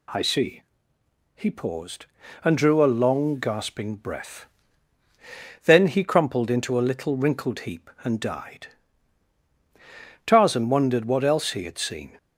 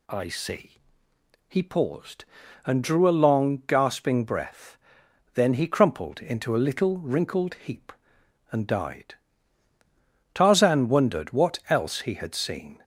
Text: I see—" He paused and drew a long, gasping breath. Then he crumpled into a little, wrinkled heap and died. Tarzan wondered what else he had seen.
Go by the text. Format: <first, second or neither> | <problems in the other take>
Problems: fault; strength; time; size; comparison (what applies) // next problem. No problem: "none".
neither | none